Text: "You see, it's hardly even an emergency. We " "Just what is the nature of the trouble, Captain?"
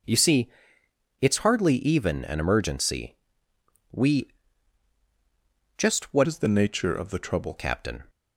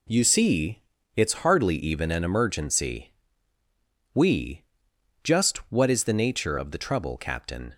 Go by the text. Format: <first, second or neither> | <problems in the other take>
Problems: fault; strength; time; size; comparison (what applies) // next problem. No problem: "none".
second | changes voice from "is" to "trouble"; from 6.2 to 7.5 s; 1.3 s long